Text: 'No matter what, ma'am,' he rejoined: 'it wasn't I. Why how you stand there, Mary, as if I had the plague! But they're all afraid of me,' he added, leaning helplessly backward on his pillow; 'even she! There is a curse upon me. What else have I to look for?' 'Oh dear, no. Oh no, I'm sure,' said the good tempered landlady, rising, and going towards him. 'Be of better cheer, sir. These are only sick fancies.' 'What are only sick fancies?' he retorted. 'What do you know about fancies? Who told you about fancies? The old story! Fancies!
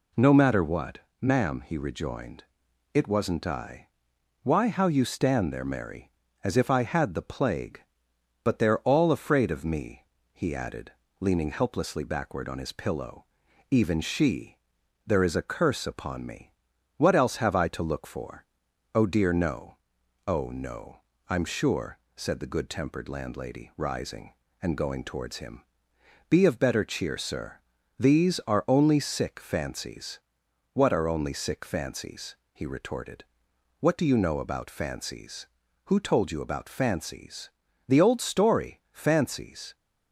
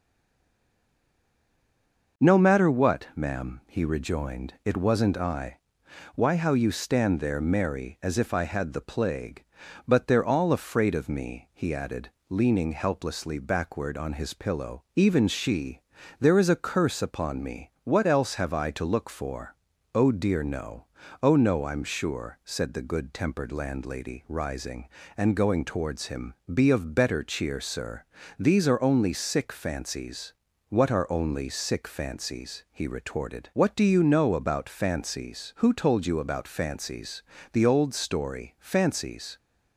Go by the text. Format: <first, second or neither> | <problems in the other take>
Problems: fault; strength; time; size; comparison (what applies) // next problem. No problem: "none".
first | stays silent before the first word; until 2.1 s; 2.1 s long